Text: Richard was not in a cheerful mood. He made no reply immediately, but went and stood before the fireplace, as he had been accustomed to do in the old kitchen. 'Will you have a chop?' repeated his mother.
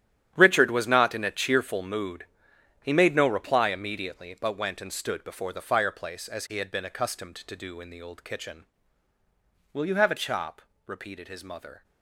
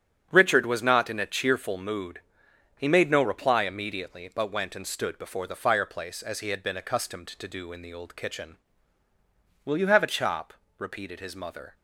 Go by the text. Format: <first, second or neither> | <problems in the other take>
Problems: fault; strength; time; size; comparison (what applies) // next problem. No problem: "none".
second | gets quieter; strong; throughout; 14 dB // starts louder than the rest; strong; until 1.3 s; 10.5 dB; strong in the second